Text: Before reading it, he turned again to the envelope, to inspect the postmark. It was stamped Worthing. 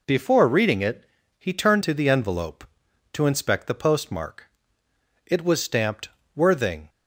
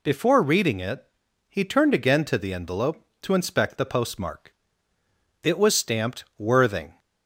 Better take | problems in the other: second | skips "again"; at 1.8 s // pauses between "stamped" and "Worthing"; slight; at 6.0 s; 0.26 s long; slight in the second

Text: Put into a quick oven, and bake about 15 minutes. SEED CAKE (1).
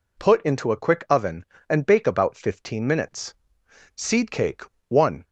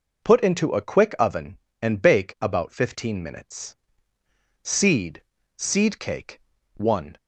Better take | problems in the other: first | says "SEED" twice; at 5.5 s

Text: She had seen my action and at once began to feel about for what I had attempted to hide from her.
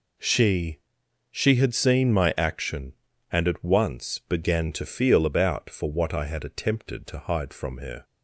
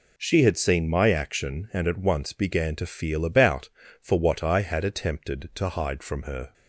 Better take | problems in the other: second | says "She" twice; at 1.2 s

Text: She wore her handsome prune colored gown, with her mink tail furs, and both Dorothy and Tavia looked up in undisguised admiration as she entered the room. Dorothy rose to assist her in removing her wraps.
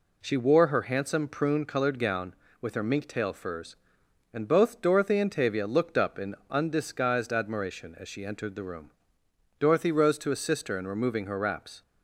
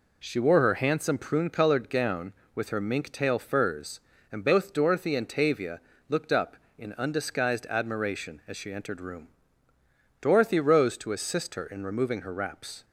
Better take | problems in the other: first | pauses between "Tavia" and "looked"; slight; at 5.8 s; 0.28 s long // skips "the"; at 9.0 s

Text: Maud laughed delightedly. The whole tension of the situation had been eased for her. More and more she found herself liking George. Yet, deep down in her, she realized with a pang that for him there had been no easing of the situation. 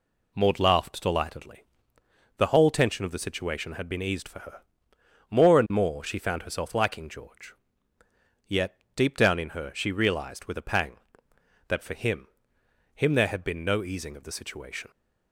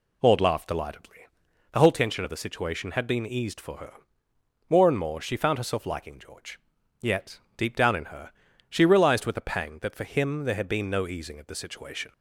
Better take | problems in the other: second | says "him" twice; at 12.9 s

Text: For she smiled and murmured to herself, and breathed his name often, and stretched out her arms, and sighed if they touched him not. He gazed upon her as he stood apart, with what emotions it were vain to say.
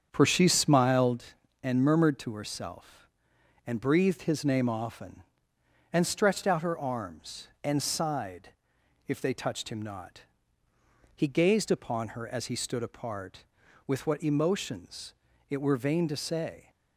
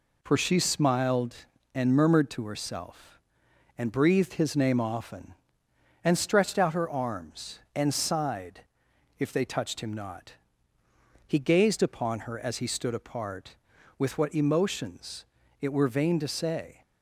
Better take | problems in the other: second | starts louder than the rest; strong; until 1.3 s; 7.5 dB // pauses between "sighed" and "if"; noticeable; at 8.4 s; 0.58 s long; noticeable in the second // pauses between "emotions" and "it"; slight; at 15.1 s; 0.36 s long; slight in the second

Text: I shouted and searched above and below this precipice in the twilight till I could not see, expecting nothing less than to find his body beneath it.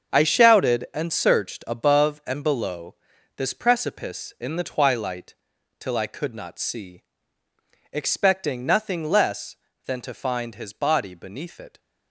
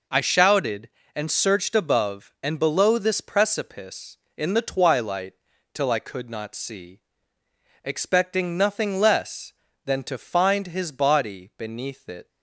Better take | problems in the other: second | gets quieter; strong; throughout; 10.5 dB // pauses between "below" and "this"; at 2.9 s; 0.42 s long // pauses between "twilight" and "till"; at 5.3 s; 0.44 s long; also in the second

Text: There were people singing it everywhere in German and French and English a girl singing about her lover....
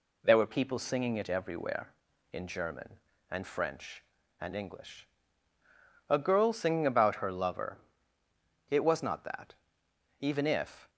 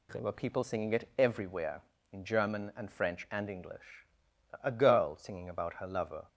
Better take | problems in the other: second | pauses between "English" and "a"; at 5.0 s; 1.0 s long; noticeable in the second // goes on to say "It was not that even if"; strong; from 8.6 s on; 2.2 s long

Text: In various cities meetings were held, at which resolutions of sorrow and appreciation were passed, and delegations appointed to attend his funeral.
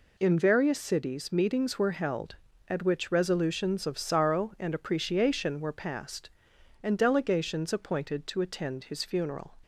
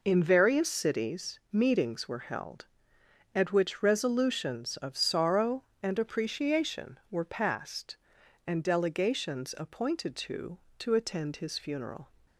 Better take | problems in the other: first | says "to" twice; at 10.7 s

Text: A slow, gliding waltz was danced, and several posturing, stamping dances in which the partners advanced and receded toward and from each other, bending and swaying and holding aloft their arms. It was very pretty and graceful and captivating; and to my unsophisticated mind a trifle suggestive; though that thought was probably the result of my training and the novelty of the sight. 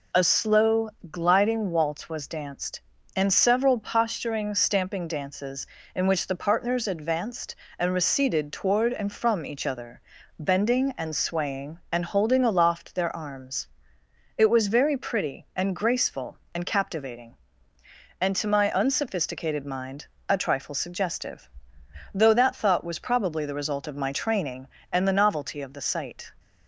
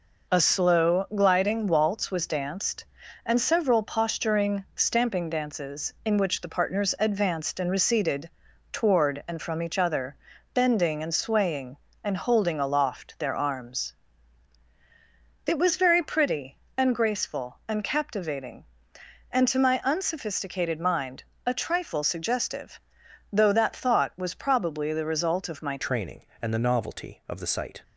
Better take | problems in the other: first | pauses between "receded" and "toward"; at 8.2 s; 0.40 s long // pauses between "mind" and "a"; slight; at 21.2 s; 0.22 s long; slight in the first // changes voice at "training"; from 25.7 s on; 2.1 s long

